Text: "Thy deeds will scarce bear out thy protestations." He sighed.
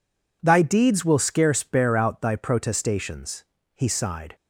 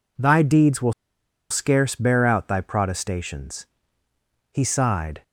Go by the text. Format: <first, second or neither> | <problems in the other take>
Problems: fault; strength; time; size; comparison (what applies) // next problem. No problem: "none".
first | pauses between "will" and "scarce"; noticeable; at 0.9 s; 0.57 s long